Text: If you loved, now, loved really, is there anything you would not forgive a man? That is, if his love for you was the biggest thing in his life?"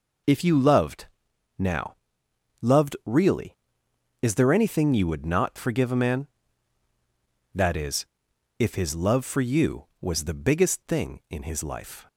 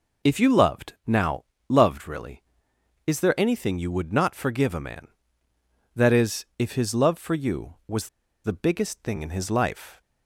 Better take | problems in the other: first | pauses between "was" and "the"; at 8.0 s; 0.38 s long

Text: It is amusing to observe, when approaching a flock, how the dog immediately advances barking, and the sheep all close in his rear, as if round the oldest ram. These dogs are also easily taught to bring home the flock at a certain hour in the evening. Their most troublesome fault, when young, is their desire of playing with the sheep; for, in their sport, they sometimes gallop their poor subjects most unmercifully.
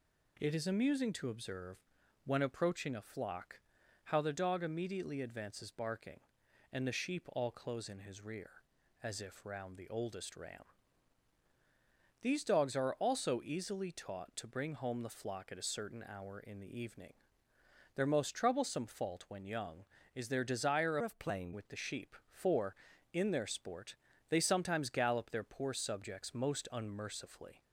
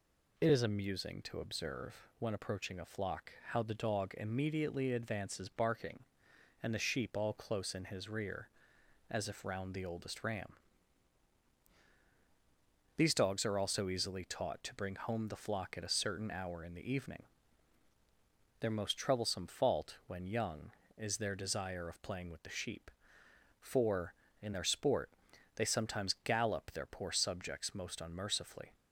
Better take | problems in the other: second | changes voice from "of" to "playing"; from 21.0 to 21.5 s; 0.5 s long

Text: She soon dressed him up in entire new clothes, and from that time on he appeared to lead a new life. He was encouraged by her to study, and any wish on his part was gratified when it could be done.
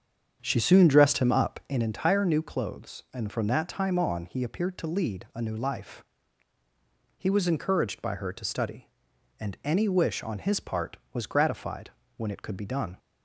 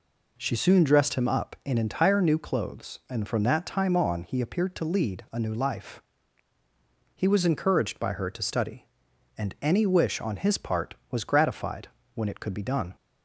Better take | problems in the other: second | starts louder than the rest; strong; until 1.8 s; 8 dB // pauses between "gratified" and "when"; slight; at 11.9 s; 0.26 s long; slight in the second

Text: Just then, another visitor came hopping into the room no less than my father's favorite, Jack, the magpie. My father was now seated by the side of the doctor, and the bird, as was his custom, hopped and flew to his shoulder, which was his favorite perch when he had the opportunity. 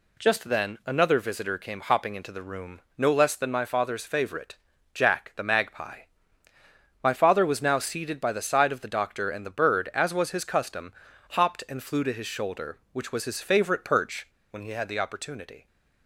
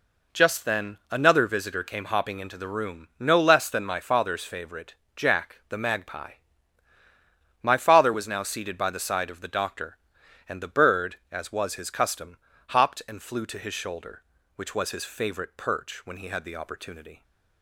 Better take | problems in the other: second | pauses between "room" and "no"; slight; at 2.7 s; 0.16 s long // pauses between "perch" and "when"; slight; at 14.2 s; 0.24 s long

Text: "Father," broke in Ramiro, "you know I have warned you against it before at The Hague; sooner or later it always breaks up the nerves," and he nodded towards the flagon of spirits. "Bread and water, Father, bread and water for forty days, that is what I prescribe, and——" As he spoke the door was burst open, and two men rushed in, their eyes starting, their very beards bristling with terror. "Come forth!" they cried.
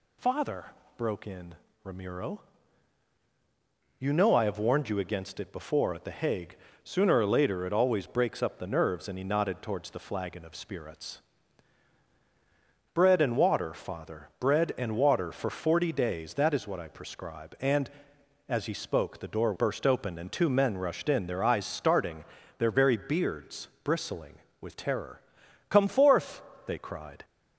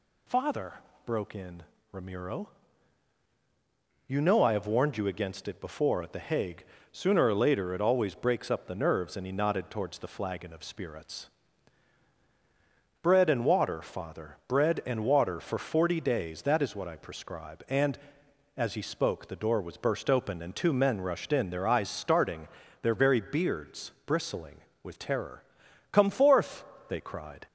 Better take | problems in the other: second | pauses between "in" and "Ramiro"; slight; at 1.5 s; 0.28 s long; slight in the second // skips "was"; at 19.5 s // pauses between "beards" and "bristling"; slight; at 23.6 s; 0.16 s long; slight in the second

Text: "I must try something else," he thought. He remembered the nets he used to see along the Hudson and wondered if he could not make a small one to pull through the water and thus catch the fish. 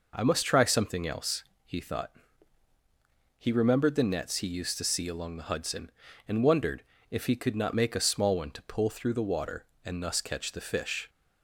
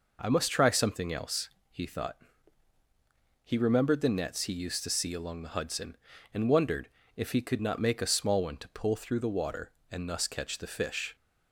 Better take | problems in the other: neither | pauses between "wondered" and "if"; slight; the same in both

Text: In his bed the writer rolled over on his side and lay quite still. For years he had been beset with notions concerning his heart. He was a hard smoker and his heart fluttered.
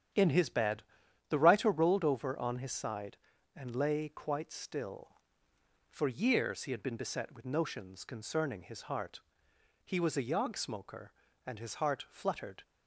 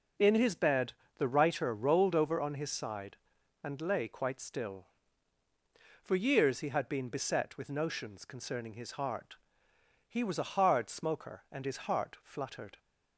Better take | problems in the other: second | starts louder than the rest; strong; until 1.6 s; 9 dB // pauses between "bed" and "the"; noticeable; at 0.8 s; 0.48 s long; slight in the second // says "yog" for "hard"; at 10.2 s

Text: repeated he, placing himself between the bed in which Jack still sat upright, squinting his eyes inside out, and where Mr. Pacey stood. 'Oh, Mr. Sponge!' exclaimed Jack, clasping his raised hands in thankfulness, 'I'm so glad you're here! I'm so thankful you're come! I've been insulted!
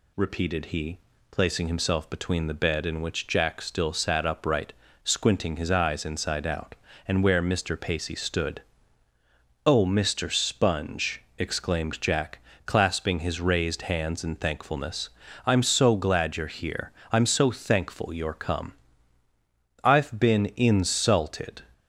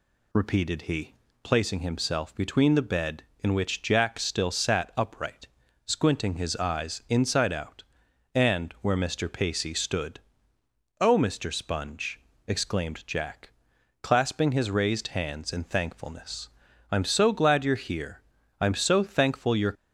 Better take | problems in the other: first | stops before "come I've been insulted"; at 19.7 s

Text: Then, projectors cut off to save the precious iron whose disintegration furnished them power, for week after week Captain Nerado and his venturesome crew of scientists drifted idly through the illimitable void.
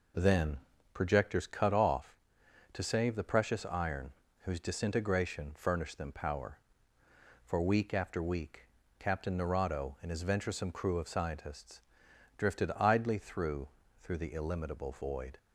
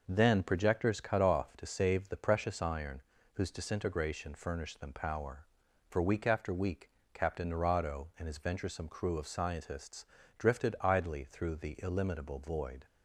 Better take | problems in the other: second | pauses between "iron" and "whose"; slight; at 4.1 s; 0.32 s long; slight in the second // pauses between "week" and "Captain"; slight; at 8.6 s; 0.32 s long; slight in the second // pauses between "scientists" and "drifted"; noticeable; at 11.8 s; 0.56 s long; slight in the second // says "through" twice; at 14.0 s

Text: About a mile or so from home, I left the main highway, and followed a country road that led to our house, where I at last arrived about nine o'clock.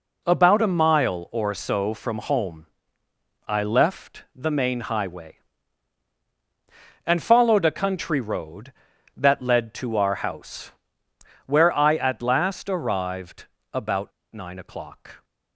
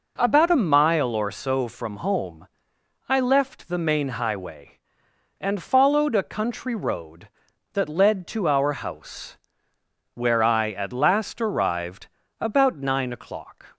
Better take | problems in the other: second | pauses between "arrived" and "about"; slight; at 13.4 s; 0.26 s long; slight in the second // pauses between "about" and "nine"; slight; at 14.1 s; 0.22 s long

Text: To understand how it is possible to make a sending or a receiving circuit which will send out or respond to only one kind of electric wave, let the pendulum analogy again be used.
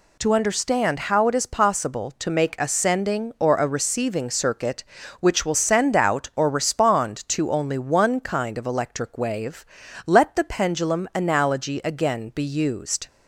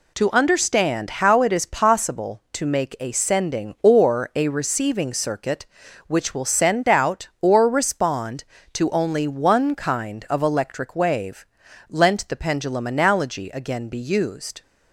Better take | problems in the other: first | says "lent" for "let"; at 11.8 s

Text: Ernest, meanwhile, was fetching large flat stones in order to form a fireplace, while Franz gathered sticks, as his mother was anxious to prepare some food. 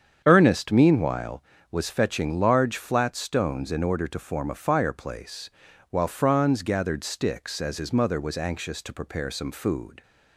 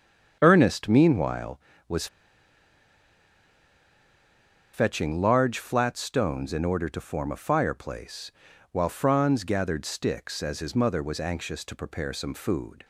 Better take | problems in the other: first | starts louder than the rest; strong; until 1.4 s; 8 dB; strong in the first // pauses between "was" and "fetching"; strong; at 2.0 s; 2.6 s long

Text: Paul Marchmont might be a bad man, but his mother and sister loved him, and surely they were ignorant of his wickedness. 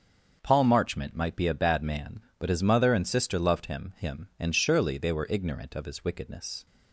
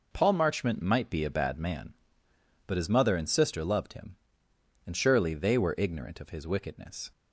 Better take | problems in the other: second | starts louder than the rest; until 1.4 s; 6.5 dB // says "him" twice; at 3.9 s

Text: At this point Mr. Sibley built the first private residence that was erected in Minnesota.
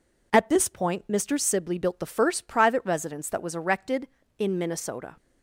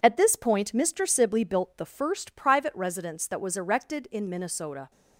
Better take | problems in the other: neither | none

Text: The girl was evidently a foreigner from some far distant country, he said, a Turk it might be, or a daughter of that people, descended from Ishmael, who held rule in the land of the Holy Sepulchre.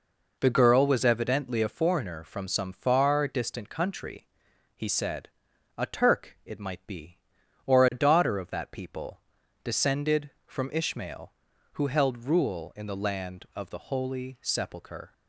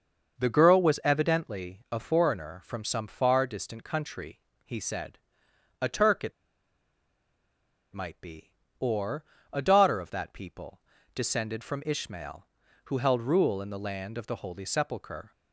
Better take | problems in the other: first | starts louder than the rest; noticeable; until 1.4 s; 6 dB // pauses between "it" and "might"; strong; at 6.3 s; 1.6 s long // pauses between "or" and "a"; slight; at 9.2 s; 0.30 s long

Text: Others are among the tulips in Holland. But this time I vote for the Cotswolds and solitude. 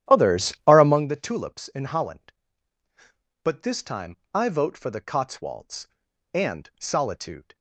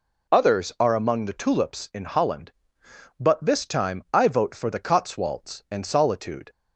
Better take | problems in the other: second | starts louder than the rest; strong; until 1.1 s; 11.5 dB // pauses between "time" and "I"; slight; at 4.1 s; 0.18 s long

